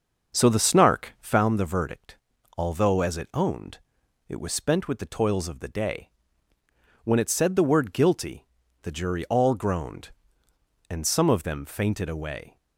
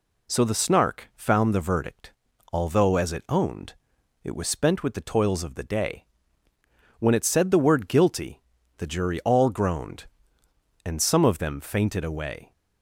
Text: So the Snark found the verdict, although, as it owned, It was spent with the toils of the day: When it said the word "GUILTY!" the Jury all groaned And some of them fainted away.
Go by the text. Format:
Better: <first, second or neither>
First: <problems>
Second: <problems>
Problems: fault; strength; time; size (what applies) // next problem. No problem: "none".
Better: second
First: starts louder than the rest; until 1.5 s; 6.5 dB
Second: none